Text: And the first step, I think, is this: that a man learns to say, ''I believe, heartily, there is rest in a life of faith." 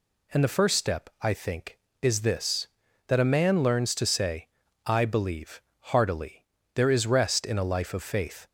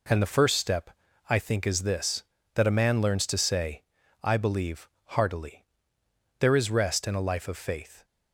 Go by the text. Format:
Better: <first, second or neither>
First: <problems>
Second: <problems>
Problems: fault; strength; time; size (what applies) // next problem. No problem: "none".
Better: neither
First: none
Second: none